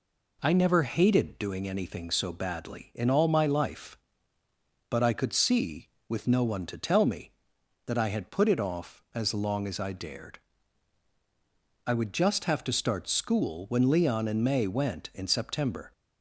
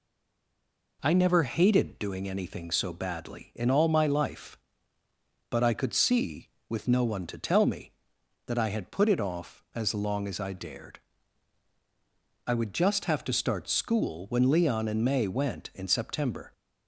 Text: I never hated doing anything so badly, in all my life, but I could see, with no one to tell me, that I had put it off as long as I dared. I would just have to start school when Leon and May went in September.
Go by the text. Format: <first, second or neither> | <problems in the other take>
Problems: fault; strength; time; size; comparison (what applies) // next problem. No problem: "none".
first | stays silent before the first word; until 0.9 s; 0.9 s long